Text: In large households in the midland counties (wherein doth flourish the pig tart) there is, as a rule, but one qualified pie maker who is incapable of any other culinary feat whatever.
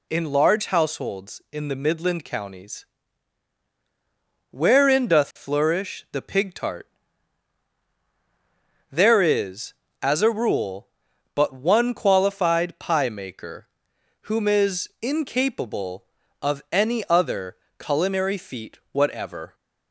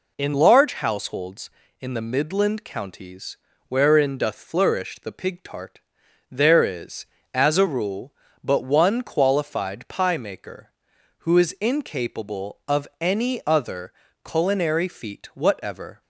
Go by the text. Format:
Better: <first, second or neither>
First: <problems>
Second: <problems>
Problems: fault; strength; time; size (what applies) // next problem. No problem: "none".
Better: second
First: says "whom" for "who"; at 14.2 s // pauses between "other" and "culinary"; slight; at 17.5 s; 0.22 s long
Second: pauses between "other" and "culinary"; slight; at 13.9 s; 0.32 s long